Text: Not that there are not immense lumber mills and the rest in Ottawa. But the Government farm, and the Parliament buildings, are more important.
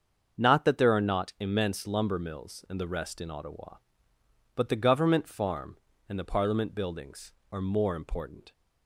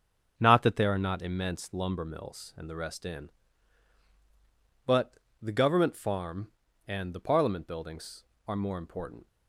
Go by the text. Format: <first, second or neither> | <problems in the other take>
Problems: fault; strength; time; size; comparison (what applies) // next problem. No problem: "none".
first | starts louder than the rest; strong; until 1.3 s; 7 dB; also in the first // skips "Ottawa"; at 4.0 s // pauses between "But" and "the"; slight; at 5.1 s; 0.24 s long